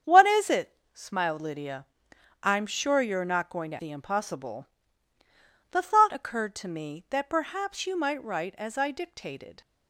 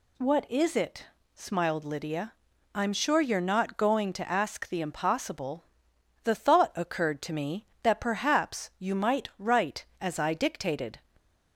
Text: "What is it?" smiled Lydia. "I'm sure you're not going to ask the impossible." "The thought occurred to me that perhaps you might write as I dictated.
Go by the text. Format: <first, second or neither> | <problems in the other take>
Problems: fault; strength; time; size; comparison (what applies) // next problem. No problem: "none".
second | starts louder than the rest; strong; until 1.2 s; 7.5 dB // skips "ask"; at 3.7 s